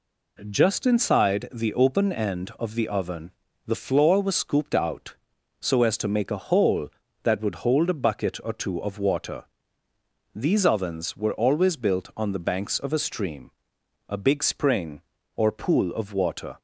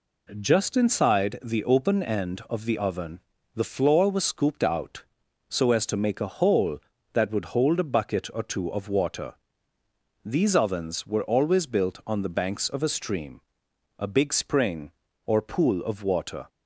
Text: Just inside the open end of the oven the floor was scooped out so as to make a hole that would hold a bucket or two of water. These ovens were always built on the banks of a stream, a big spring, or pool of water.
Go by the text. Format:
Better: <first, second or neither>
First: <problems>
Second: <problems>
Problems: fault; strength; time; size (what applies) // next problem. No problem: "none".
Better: neither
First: pauses between "oven" and "the"; slight; at 3.3 s; 0.34 s long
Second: pauses between "oven" and "the"; slight; at 3.2 s; 0.34 s long